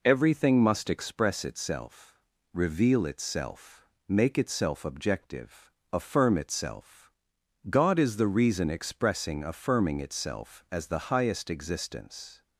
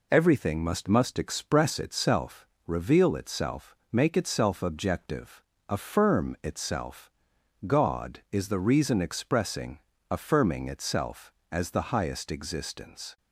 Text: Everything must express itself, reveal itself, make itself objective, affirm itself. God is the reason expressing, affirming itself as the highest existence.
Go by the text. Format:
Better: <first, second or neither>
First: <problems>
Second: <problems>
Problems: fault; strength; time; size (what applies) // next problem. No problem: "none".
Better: first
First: none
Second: says "must" twice; at 0.8 s